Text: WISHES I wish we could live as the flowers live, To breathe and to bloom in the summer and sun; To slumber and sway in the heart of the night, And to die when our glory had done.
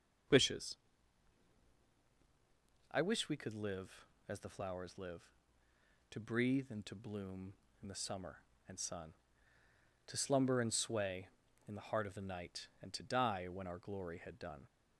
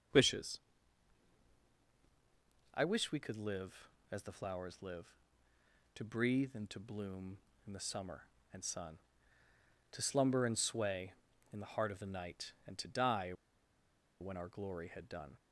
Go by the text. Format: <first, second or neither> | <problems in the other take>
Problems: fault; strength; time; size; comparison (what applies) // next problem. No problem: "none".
first | starts louder than the rest; noticeable; until 3.2 s; 6 dB; noticeable in the first // pauses between "WISHES" and "I"; strong; at 0.5 s; 2.1 s long; strong in the first // pauses between "die" and "when"; noticeable; at 13.3 s; 0.89 s long